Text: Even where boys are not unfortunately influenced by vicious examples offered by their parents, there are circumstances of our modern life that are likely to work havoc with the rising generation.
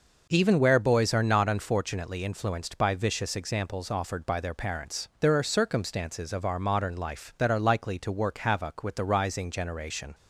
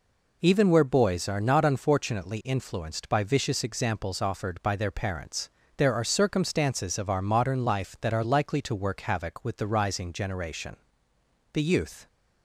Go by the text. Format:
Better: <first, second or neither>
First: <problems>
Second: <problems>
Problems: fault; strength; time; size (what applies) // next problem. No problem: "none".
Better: first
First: none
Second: goes on to say "The youth"; from 11.5 s on; 0.54 s long